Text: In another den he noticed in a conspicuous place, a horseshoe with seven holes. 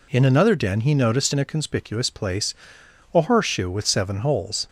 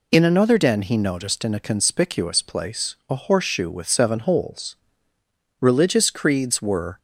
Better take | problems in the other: first | goes on to say "Religious creeds were"; from 5.5 s on; 1.3 s long

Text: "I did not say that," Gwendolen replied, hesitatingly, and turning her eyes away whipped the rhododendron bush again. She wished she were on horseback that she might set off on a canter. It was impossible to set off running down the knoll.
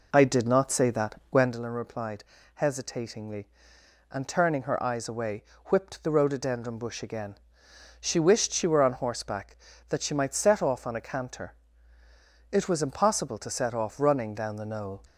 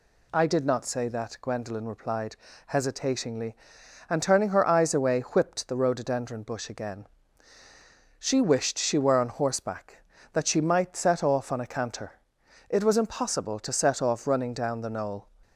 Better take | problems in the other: second | starts louder than the rest; noticeable; until 1.6 s; 4 dB // pauses between "away" and "whipped"; slight; at 5.4 s; 0.22 s long

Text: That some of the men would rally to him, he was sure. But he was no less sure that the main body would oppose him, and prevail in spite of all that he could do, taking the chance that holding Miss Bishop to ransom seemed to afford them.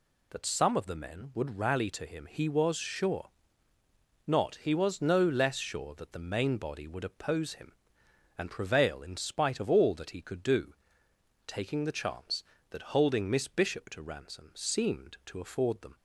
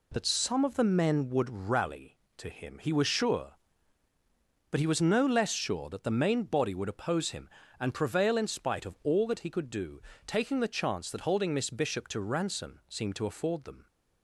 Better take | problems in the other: second | says "Not" for "But"; at 4.2 s

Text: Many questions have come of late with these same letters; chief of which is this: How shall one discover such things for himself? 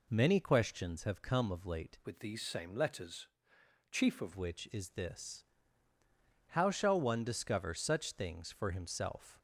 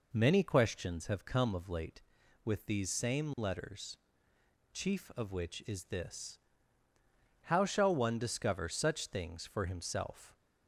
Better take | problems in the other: second | changes voice from "with" to "of"; from 2.0 to 4.3 s; 2.3 s long

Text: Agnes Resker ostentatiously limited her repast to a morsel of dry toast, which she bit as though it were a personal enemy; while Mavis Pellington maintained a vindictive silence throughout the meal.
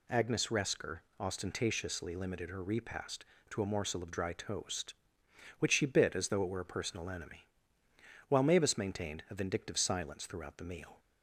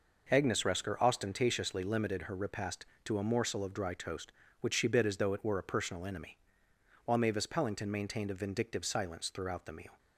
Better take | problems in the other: second | pauses between "Resker" and "ostentatiously"; slight; at 0.9 s; 0.18 s long // skips "Pellington"; at 8.7 s

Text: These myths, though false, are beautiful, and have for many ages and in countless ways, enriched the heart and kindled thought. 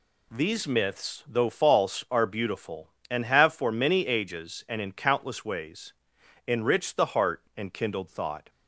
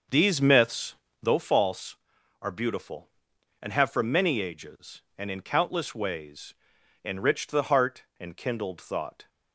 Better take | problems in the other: first | starts louder than the rest; until 1.5 s; 6.5 dB

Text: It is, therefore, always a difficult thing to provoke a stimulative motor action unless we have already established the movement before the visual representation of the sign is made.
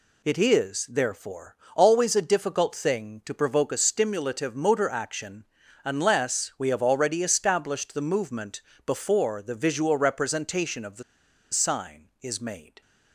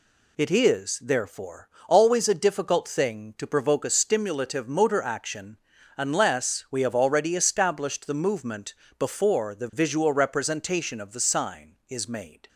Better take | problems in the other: second | pauses between "action" and "unless"; at 5.4 s; 0.40 s long; also in the second // pauses between "movement" and "before"; slight; at 8.6 s; 0.26 s long; slight in the second // pauses between "the" and "sign"; noticeable; at 11.0 s; 0.49 s long

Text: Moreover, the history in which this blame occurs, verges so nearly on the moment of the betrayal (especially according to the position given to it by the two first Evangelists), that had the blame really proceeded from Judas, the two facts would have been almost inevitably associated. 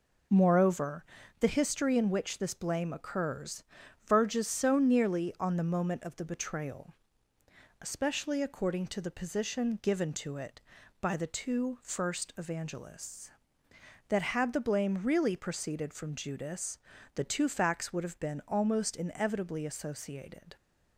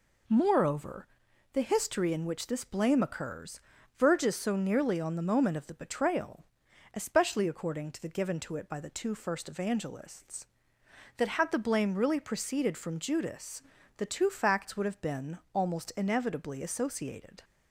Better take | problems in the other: first | skips "position"; at 8.0 s // pauses between "been" and "almost"; slight; at 15.3 s; 0.16 s long

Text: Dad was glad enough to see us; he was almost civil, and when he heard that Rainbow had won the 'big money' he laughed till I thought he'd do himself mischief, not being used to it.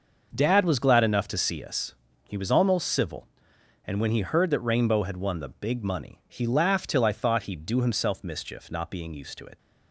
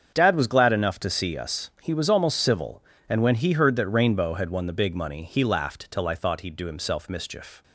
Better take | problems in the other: first | starts louder than the rest; strong; until 1.1 s; 7.5 dB; noticeable in the first // stops before "not being used to it"; at 7.6 s

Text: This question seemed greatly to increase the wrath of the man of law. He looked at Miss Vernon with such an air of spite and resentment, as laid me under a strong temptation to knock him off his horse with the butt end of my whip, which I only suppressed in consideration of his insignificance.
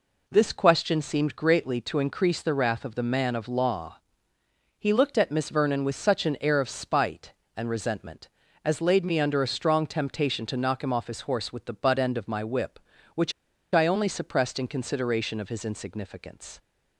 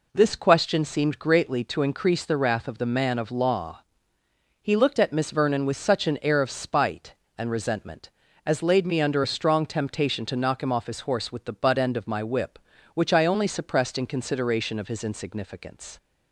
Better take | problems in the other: second | pauses between "which" and "I"; at 13.3 s; 0.40 s long

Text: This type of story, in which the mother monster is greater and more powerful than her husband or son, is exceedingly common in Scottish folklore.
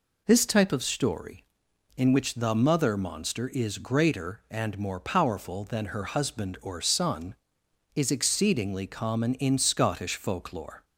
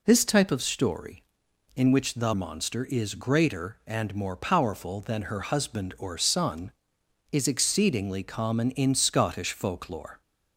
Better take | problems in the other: first | skips "mother"; at 2.3 s

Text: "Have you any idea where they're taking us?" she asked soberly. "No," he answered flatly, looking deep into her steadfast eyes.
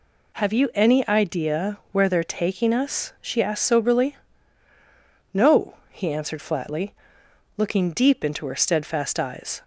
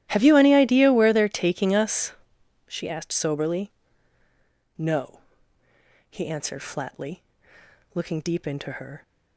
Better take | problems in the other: first | starts louder than the rest; strong; until 1.1 s; 13.5 dB // stops before "steadfast eyes"; at 9.0 s

